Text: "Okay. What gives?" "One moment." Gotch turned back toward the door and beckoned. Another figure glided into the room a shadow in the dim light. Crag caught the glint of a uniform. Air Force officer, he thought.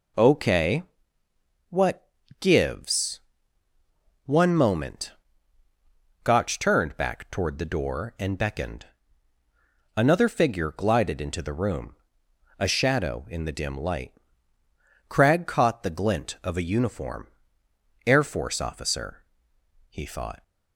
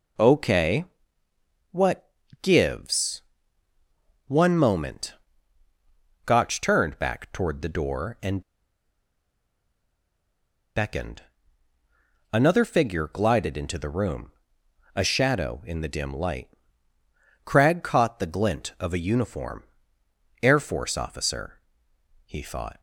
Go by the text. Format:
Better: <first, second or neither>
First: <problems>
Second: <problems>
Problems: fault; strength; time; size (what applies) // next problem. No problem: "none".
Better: first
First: pauses between "What" and "gives"; slight; at 2.0 s; 0.32 s long // pauses between "room" and "a"; noticeable; at 11.9 s; 0.62 s long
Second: pauses between "What" and "gives"; slight; at 2.1 s; 0.32 s long // pauses between "and" and "beckoned"; strong; at 8.4 s; 2.3 s long // pauses between "room" and "a"; noticeable; at 14.3 s; 0.62 s long